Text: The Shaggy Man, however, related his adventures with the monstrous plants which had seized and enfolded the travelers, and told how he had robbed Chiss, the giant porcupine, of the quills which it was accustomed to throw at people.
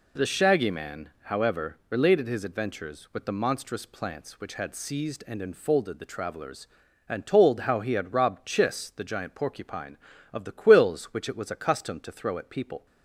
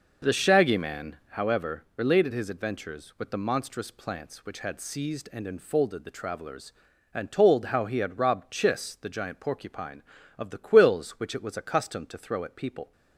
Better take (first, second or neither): first